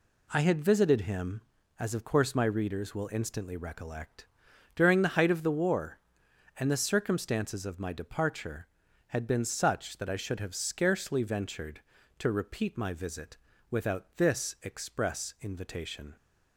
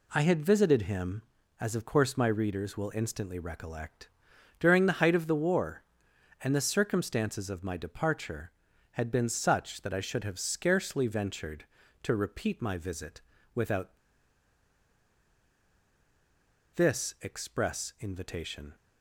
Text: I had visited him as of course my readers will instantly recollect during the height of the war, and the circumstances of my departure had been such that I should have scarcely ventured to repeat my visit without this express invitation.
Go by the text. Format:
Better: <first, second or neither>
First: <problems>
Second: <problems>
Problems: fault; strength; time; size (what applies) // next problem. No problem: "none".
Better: first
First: pauses between "recollect" and "during"; noticeable; at 4.2 s; 0.48 s long // pauses between "visit" and "without"; slight; at 13.3 s; 0.32 s long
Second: pauses between "recollect" and "during"; noticeable; at 4.0 s; 0.50 s long // pauses between "visit" and "without"; slight; at 13.2 s; 0.32 s long // pauses between "without" and "this"; strong; at 13.9 s; 2.7 s long